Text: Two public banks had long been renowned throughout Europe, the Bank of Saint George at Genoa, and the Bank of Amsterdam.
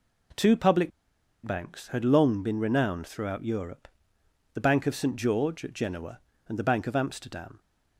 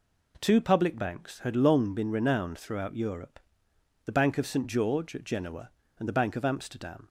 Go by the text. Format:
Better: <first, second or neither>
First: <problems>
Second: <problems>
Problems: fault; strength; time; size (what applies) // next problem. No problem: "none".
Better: second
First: pauses between "public" and "banks"; noticeable; at 0.9 s; 0.55 s long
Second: none